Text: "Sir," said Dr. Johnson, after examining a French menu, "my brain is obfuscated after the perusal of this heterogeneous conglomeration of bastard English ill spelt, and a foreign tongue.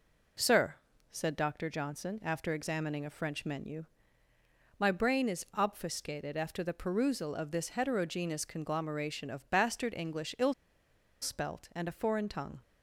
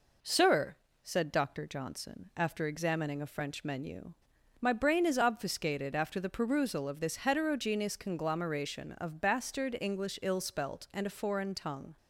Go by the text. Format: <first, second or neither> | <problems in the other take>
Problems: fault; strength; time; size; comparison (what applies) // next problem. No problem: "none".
second | pauses between "ill" and "spelt"; noticeable; at 10.5 s; 0.68 s long